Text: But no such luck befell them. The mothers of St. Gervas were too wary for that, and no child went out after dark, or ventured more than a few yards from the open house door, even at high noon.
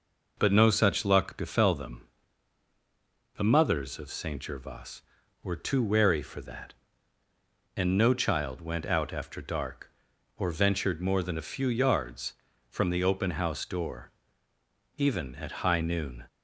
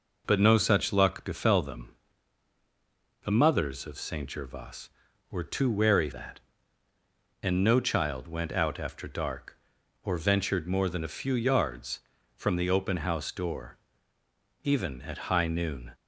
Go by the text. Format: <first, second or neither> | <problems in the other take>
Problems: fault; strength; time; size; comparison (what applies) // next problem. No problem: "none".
first | skips "for"; at 6.1 s